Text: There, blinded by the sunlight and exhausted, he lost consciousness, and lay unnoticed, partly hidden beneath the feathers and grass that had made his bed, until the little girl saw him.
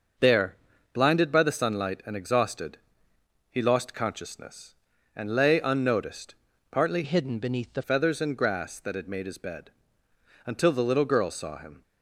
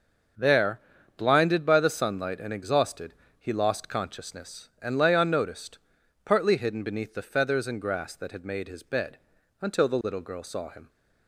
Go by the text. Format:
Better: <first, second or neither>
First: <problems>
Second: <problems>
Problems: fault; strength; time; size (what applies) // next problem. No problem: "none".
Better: second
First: starts louder than the rest; noticeable; until 1.5 s; 6 dB // changes voice from "hidden" to "the"; from 7.0 to 7.8 s; 0.8 s long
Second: starts louder than the rest; until 1.7 s; 6.5 dB